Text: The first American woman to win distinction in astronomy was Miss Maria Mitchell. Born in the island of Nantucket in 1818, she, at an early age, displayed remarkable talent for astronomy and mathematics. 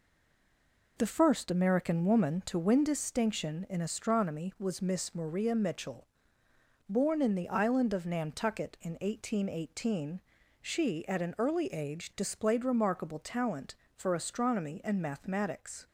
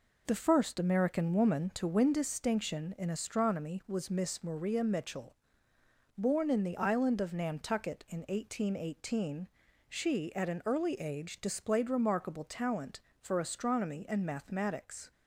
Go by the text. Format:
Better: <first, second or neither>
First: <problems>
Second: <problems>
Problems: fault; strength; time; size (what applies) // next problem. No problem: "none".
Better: second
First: stays silent before the first word; until 0.9 s; 0.9 s long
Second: none